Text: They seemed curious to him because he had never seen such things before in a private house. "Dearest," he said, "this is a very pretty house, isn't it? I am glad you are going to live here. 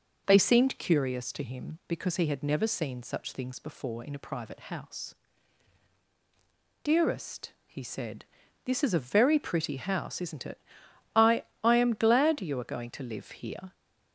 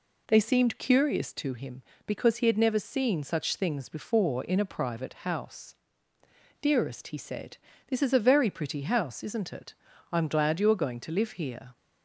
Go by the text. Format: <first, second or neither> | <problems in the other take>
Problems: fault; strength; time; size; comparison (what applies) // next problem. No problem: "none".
second | says "I" twice; at 11.6 s